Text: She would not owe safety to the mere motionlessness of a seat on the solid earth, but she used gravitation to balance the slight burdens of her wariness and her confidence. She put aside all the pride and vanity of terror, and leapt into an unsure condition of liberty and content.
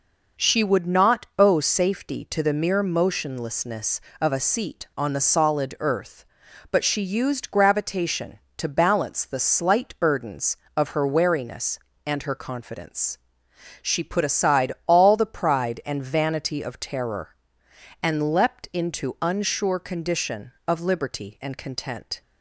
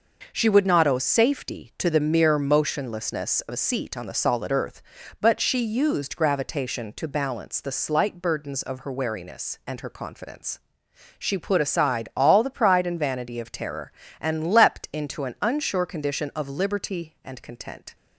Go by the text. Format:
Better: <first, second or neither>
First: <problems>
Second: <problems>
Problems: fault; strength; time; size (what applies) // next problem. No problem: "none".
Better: second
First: pauses between "aside" and "all"; slight; at 14.7 s; 0.16 s long // skips "an"; at 19.1 s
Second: none